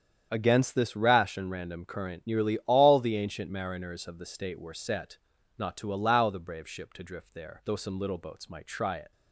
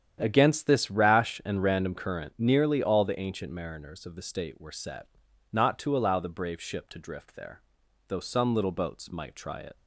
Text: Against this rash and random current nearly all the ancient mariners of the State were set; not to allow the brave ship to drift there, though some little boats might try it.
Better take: neither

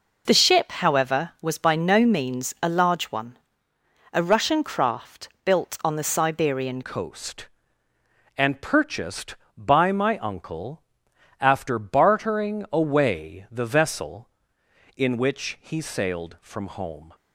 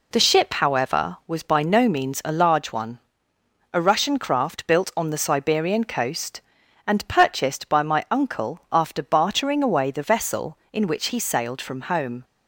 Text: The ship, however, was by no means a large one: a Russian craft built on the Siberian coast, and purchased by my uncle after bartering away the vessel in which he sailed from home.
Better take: second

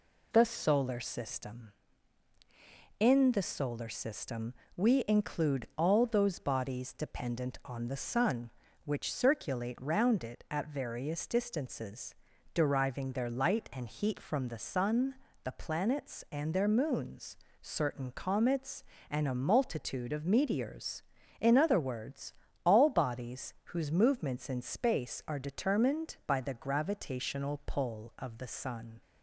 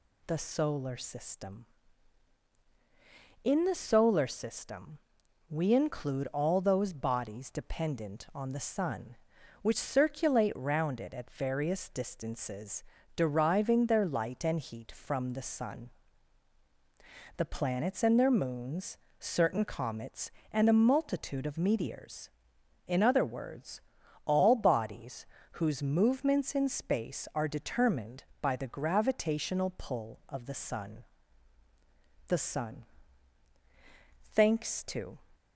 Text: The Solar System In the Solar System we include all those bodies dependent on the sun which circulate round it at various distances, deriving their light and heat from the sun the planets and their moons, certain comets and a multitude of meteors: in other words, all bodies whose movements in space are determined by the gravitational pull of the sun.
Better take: first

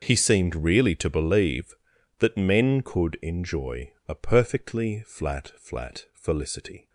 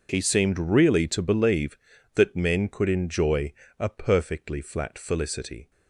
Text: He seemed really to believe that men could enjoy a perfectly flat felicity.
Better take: second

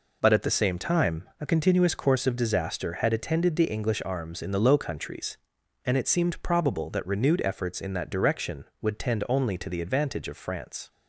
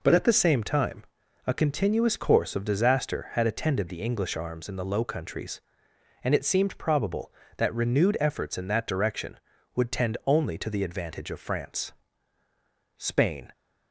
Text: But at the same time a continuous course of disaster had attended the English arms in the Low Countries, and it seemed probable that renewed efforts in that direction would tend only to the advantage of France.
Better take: first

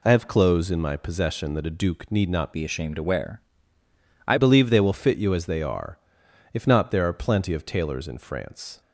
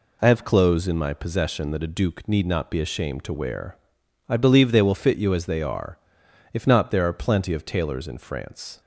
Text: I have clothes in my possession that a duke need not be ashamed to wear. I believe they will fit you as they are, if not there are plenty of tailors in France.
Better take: second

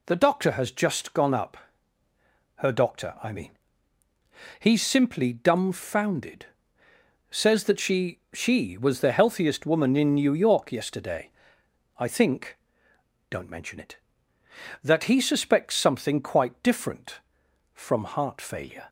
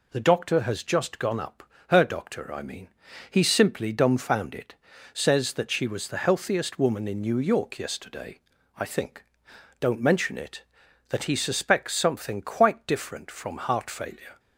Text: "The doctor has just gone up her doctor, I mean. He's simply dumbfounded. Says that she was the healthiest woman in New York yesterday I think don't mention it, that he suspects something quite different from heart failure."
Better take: second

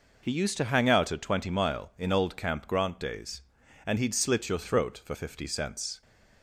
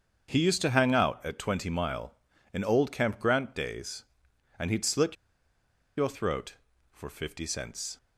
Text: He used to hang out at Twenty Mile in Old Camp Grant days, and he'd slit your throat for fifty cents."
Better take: first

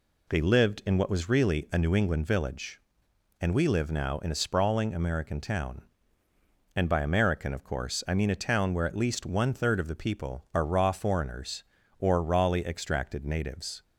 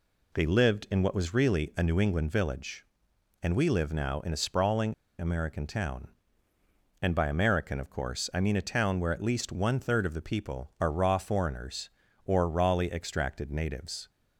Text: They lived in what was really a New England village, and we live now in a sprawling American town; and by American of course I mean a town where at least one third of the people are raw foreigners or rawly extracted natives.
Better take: first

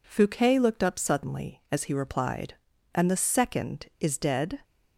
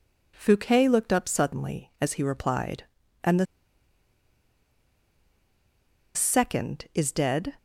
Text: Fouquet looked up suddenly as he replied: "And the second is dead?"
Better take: first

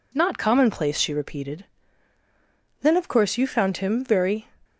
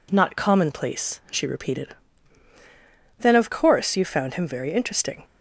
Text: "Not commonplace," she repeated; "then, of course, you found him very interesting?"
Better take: second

